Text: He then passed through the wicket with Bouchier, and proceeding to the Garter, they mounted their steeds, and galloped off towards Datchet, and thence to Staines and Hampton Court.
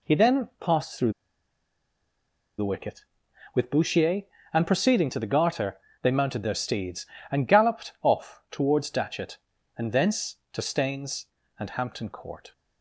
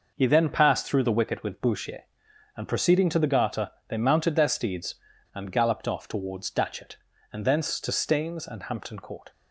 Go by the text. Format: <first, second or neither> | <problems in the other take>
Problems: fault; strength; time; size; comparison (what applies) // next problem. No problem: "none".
second | pauses between "through" and "the"; strong; at 1.1 s; 1.4 s long